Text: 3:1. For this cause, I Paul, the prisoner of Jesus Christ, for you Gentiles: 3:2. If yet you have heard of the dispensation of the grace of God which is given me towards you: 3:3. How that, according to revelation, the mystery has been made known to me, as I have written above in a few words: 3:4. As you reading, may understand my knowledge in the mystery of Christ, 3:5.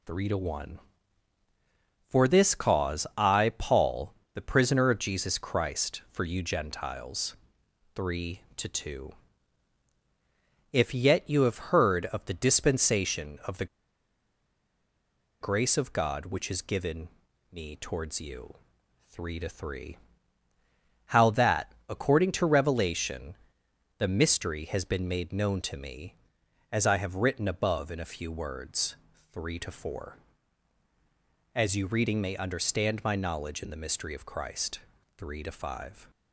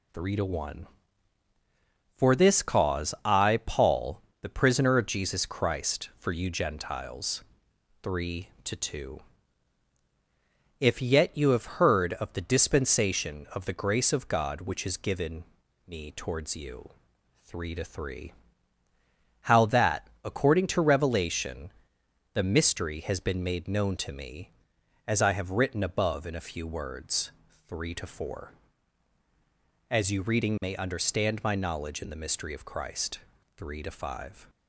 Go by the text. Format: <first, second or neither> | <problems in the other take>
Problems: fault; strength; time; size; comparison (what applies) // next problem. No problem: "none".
second | pauses between "the" and "grace"; strong; at 13.6 s; 1.7 s long // pauses between "given" and "me"; at 17.0 s; 0.44 s long; also in the second